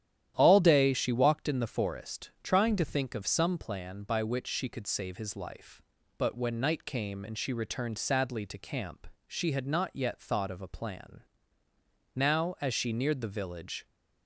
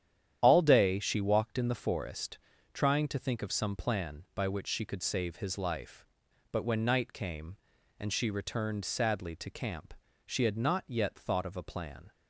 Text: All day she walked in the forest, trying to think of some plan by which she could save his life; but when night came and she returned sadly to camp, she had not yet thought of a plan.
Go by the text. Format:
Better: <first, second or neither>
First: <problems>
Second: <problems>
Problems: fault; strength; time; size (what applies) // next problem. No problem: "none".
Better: second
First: starts louder than the rest; strong; until 1.3 s; 11 dB // goes on to say "Now as she neared the village"; strong; from 12.1 s on; 1.7 s long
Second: starts louder than the rest; strong; until 1.4 s; 10 dB